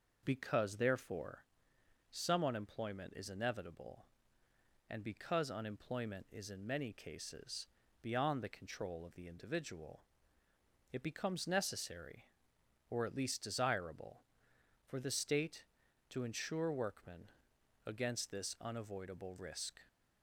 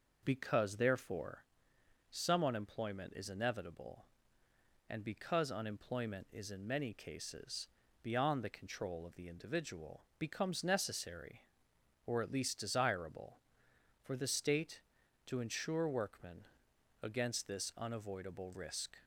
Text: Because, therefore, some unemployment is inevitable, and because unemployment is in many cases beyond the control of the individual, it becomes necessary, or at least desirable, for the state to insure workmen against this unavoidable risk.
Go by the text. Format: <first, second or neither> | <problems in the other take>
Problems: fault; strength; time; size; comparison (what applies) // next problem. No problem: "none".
first | pauses between "cases" and "beyond"; slight; at 7.6 s; 0.34 s long; slight in the first // skips "it"; at 10.1 s // pauses between "workmen" and "against"; noticeable; at 16.4 s; 0.60 s long; noticeable in the first